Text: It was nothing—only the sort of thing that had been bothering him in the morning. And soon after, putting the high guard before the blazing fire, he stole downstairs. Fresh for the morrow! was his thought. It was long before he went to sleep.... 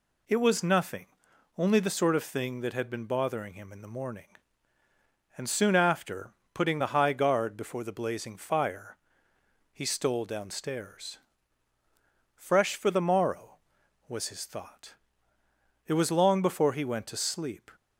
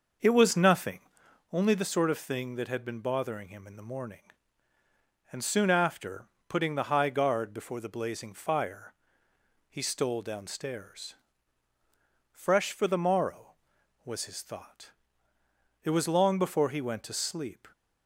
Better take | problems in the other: first | starts louder than the rest; until 1.5 s; 6 dB

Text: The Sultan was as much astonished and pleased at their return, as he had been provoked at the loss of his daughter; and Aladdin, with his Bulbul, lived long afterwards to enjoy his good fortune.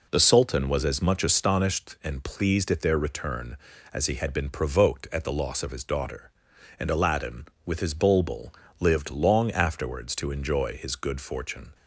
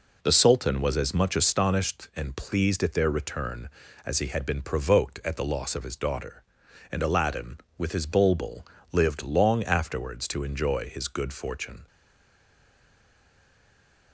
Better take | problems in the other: first | stays silent after the last word; from 11.8 s on; 2.3 s long

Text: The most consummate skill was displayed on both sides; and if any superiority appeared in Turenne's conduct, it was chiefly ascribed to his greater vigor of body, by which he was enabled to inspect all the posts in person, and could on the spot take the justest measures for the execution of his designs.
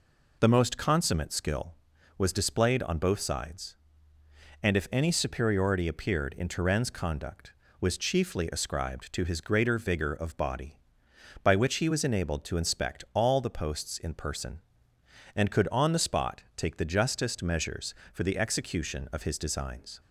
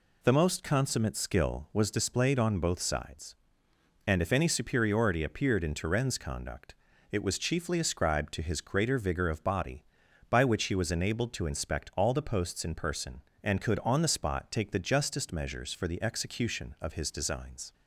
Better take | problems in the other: second | skips "it"; at 7.6 s

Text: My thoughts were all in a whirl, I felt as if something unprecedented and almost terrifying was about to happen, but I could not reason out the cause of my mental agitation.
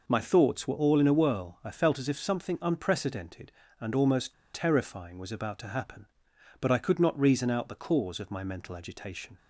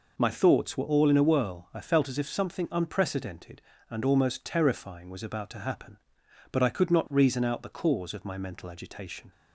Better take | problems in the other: second | pauses between "almost" and "terrifying"; slight; at 4.3 s; 0.20 s long

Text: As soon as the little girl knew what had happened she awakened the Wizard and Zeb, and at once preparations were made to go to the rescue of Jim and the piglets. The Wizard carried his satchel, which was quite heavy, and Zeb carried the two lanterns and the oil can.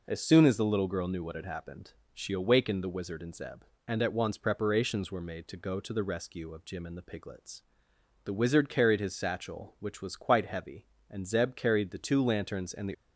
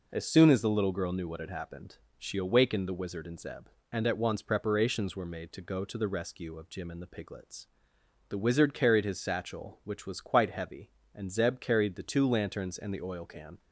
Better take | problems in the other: second | pauses between "happened" and "she"; slight; at 1.9 s; 0.20 s long; slight in the second // stops before "oil can"; at 12.9 s

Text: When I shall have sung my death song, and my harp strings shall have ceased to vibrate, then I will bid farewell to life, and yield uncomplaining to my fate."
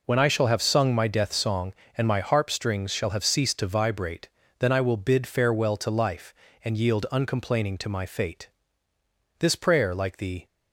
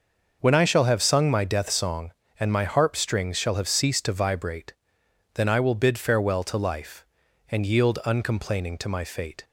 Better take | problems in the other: second | goes on to say "This prayer like the"; noticeable; from 9.3 s on; 1.0 s long

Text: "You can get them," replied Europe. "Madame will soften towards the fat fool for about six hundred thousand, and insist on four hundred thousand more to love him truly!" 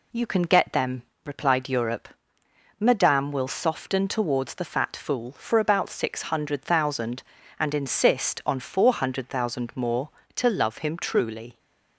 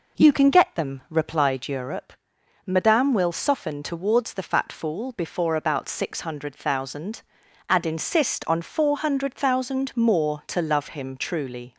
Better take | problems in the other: first | says "before" for "for"; at 5.1 s

